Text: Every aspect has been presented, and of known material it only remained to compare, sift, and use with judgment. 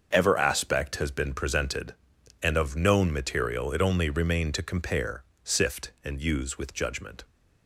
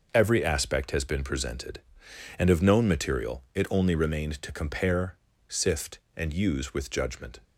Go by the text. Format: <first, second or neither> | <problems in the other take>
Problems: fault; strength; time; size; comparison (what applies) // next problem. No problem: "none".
second | starts louder than the rest; until 1.1 s; 6.5 dB // says "Ever" for "Every"; at 0.1 s